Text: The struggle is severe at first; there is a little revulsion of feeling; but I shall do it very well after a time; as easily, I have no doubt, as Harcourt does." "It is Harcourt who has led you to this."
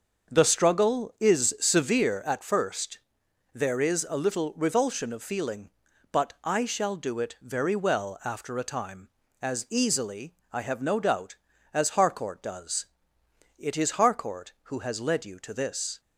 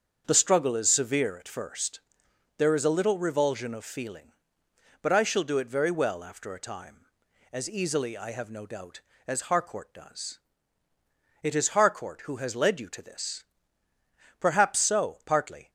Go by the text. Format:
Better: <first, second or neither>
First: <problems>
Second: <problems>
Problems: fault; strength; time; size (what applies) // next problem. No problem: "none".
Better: first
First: starts louder than the rest; until 1.3 s; 6.5 dB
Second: starts louder than the rest; until 1.2 s; 7 dB // goes on to say "Perhaps so partly"; noticeable; from 14.3 s on; 1.3 s long